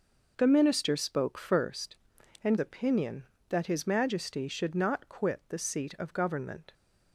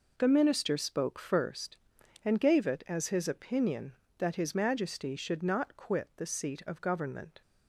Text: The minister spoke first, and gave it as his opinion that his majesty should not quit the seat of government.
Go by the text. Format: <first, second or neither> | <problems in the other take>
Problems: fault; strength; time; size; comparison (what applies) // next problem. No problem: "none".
second | skips "gave it as his"; at 2.5 s